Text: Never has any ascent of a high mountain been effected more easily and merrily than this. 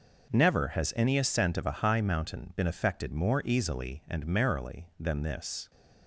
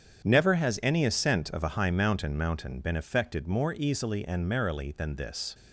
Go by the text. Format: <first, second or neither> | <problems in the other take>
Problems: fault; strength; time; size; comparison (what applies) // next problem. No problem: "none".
first | starts louder than the rest; strong; until 1.2 s; 8 dB // says "mountain" twice; at 2.3 s